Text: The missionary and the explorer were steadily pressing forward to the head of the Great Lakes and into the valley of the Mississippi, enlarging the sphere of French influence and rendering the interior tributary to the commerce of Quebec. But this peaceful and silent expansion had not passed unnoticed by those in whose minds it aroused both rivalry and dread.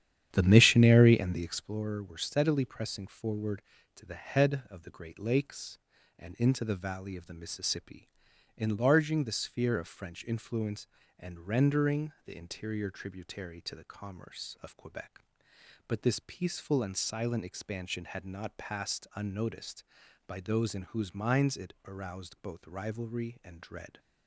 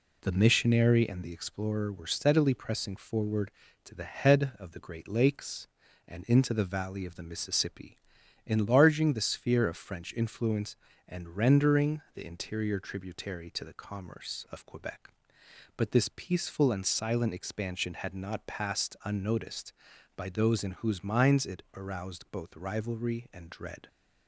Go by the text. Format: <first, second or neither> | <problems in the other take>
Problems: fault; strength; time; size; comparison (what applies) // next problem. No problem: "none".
second | starts louder than the rest; strong; until 1.7 s; 10 dB